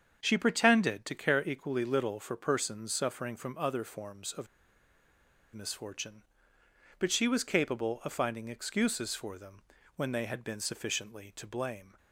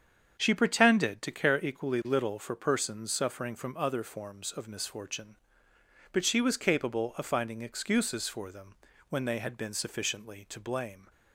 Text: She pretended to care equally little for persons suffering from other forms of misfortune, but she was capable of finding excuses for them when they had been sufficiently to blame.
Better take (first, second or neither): second